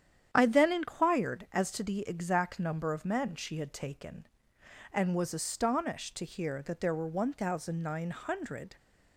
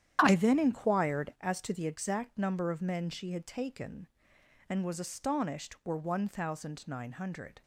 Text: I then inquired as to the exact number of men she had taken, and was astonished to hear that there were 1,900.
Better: first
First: starts louder than the rest; strong; until 1.3 s; 9.5 dB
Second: starts louder than the rest; strong; until 1.2 s; 10 dB // skips "to hear that there"; at 5.8 s

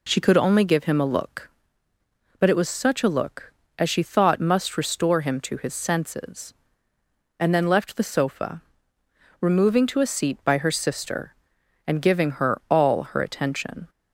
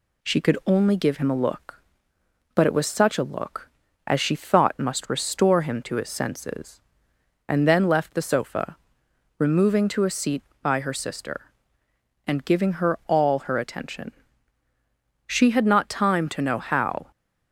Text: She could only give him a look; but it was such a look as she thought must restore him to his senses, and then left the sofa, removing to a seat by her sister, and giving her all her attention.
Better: first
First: none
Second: goes on to say "She had not time to know how"; strong; from 15.2 s on; 1.8 s long

